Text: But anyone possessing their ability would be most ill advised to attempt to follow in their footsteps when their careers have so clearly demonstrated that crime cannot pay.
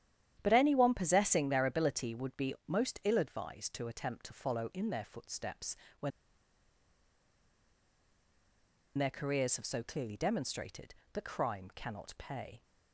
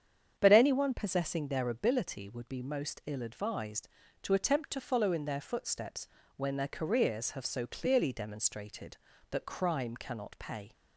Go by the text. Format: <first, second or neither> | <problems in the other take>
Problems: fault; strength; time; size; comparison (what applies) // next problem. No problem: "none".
second | starts louder than the rest; strong; until 1.4 s; 10.5 dB; strong in the second // pauses between "footsteps" and "when"; slight; at 5.7 s; 0.24 s long; slight in the second // pauses between "when" and "their"; strong; at 6.1 s; 2.8 s long